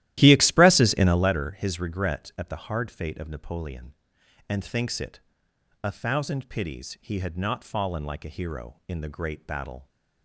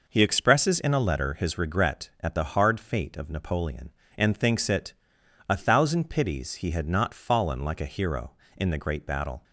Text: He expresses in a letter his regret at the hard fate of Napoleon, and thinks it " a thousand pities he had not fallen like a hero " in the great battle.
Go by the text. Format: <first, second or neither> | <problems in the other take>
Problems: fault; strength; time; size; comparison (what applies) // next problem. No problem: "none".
second | starts louder than the rest; strong; until 1.4 s; 14.5 dB